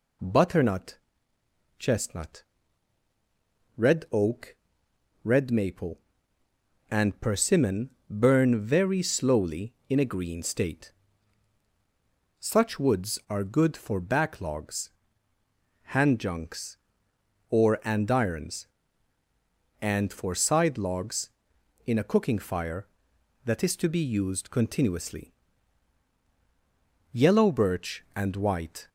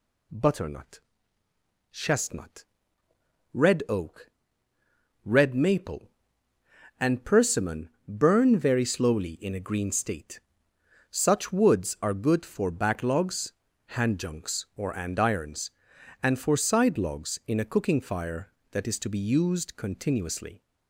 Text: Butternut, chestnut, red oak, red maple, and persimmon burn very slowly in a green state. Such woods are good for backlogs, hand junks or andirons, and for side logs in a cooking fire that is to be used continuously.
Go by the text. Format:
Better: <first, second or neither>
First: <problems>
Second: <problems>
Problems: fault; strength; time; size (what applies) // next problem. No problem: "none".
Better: second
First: pauses between "persimmon" and "burn"; slight; at 7.8 s; 0.20 s long // goes on to say "Yellow birch and white"; strong; from 27.1 s on; 1.7 s long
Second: pauses between "persimmon" and "burn"; slight; at 7.8 s; 0.18 s long